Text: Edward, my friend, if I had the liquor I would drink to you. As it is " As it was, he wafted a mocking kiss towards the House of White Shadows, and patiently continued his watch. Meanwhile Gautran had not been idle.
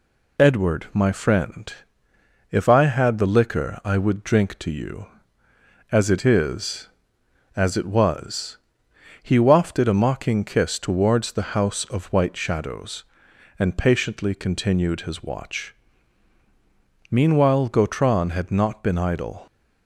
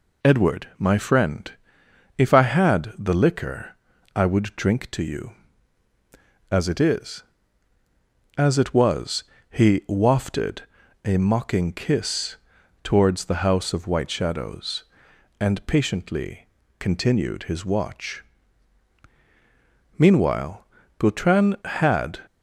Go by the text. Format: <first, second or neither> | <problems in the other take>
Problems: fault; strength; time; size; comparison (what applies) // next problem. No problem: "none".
first | pauses between "liquor" and "I"; at 3.7 s; 0.40 s long // pauses between "wafted" and "a"; at 10.6 s; 0.42 s long // pauses between "kiss" and "towards"; noticeable; at 12.3 s; 0.46 s long // pauses between "patiently" and "continued"; slight; at 16.4 s; 0.32 s long // pauses between "Meanwhile" and "Gautran"; slight; at 20.6 s; 0.32 s long // stops before "not been idle"; at 22.2 s